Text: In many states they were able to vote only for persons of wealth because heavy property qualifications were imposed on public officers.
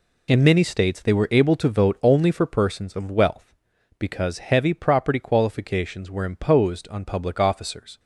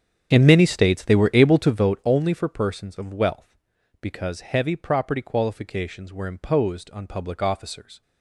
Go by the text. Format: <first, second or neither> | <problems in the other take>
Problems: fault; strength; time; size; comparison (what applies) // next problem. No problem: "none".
first | starts louder than the rest; strong; until 2.0 s; 8 dB